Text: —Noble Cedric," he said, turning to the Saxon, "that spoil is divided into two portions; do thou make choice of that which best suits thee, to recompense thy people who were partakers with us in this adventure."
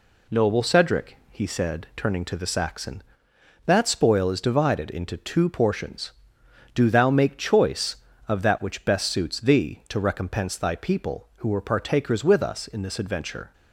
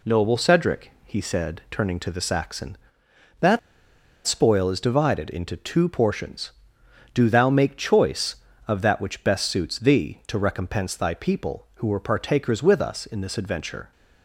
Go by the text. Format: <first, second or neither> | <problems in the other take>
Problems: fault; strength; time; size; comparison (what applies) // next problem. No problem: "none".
first | pauses between "that" and "spoil"; noticeable; at 3.5 s; 0.67 s long